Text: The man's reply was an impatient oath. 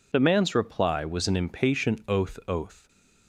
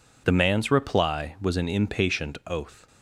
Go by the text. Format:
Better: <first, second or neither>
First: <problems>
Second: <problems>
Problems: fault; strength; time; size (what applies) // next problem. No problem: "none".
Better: second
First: says "oath" twice; at 2.4 s // stays silent after the last word; slight; from 2.7 s on; 0.5 s long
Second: none